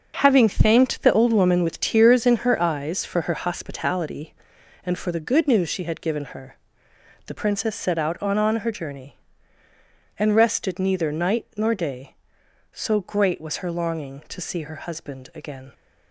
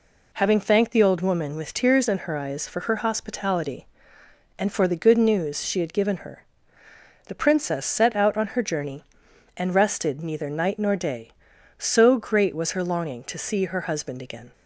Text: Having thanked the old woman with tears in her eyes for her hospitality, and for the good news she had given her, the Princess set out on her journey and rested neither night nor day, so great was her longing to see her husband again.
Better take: second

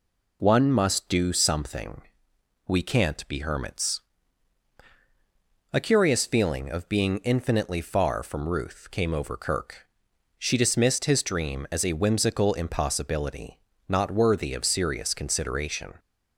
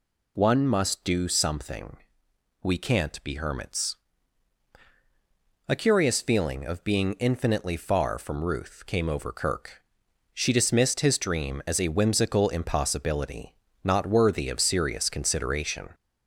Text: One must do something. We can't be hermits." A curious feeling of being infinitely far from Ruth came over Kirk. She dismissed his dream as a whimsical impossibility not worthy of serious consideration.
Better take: first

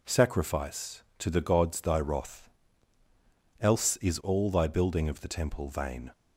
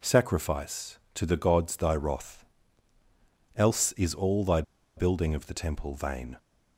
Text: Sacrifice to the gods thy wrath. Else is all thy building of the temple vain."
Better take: first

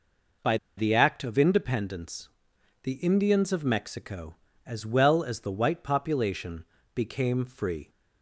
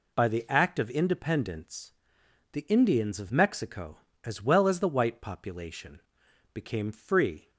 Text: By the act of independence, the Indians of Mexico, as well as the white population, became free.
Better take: second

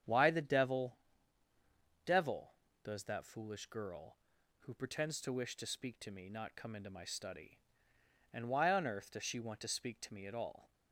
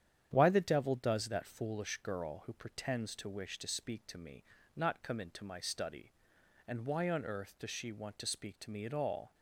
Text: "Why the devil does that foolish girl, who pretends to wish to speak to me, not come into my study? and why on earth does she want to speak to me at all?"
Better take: second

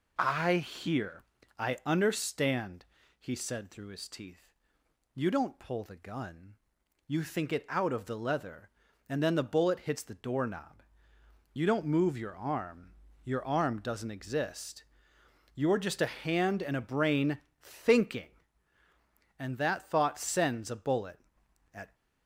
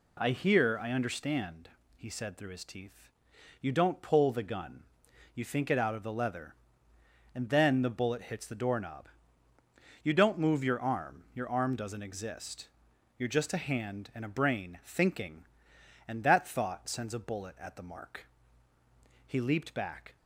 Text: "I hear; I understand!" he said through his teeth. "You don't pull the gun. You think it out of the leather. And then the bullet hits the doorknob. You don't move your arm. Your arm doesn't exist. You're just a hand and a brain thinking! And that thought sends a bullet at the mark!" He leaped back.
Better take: second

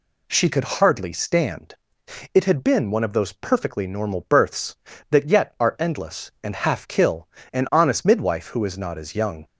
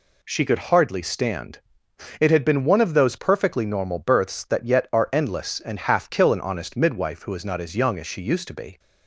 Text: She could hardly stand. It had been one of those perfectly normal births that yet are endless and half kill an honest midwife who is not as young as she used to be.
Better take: second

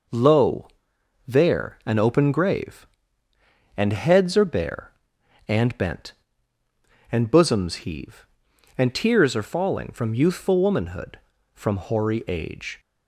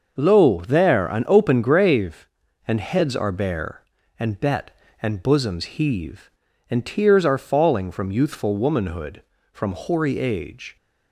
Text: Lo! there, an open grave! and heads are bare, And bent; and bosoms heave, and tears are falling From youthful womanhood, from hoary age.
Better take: first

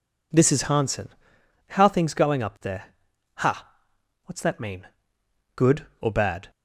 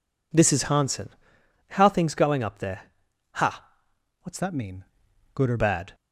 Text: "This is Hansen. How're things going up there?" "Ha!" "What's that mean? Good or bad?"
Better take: first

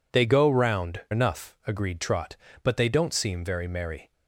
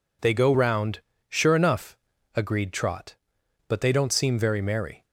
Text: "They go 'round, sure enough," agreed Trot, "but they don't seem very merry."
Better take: second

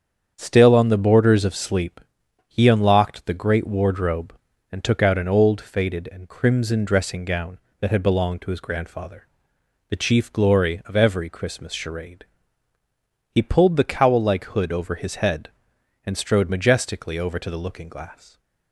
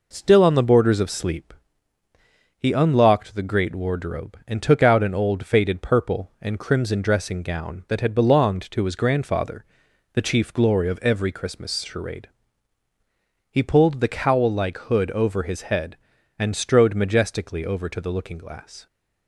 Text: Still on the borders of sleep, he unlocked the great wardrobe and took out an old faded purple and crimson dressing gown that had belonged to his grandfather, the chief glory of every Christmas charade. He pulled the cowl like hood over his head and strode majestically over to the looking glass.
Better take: second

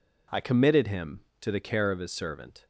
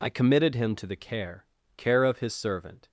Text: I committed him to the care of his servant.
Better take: first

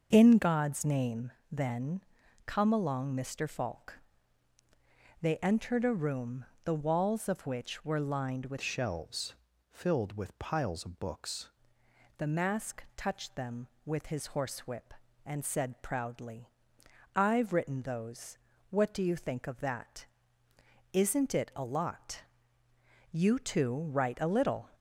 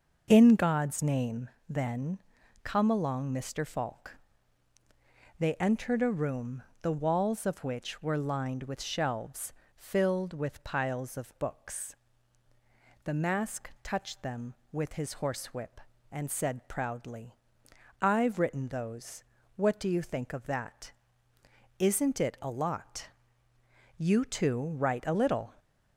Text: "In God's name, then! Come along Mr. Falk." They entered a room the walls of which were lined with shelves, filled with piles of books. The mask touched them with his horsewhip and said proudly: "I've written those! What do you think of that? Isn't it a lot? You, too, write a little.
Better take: second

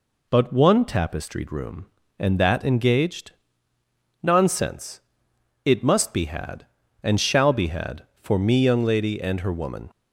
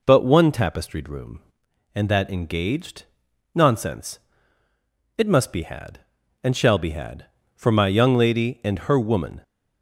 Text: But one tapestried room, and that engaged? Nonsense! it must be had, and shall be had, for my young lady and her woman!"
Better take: second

